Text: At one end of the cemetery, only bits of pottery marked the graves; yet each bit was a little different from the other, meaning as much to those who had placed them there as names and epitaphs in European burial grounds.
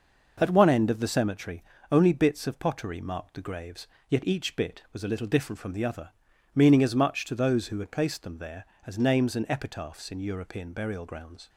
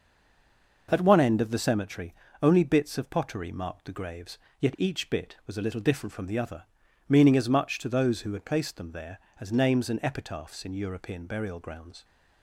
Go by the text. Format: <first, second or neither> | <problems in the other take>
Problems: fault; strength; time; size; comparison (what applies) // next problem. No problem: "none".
first | stays silent before the first word; slight; until 0.8 s; 0.8 s long